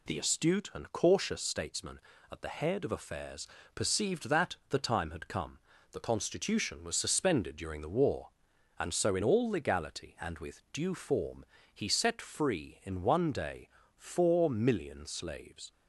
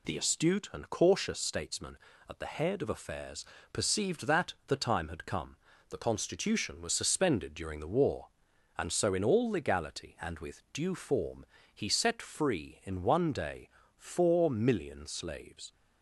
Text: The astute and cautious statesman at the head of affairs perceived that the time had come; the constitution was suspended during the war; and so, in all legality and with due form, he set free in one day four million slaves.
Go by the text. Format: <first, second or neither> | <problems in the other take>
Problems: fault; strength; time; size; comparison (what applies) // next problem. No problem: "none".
neither | pauses between "affairs" and "perceived"; slight; the same in both // pauses between "day" and "four"; slight; the same in both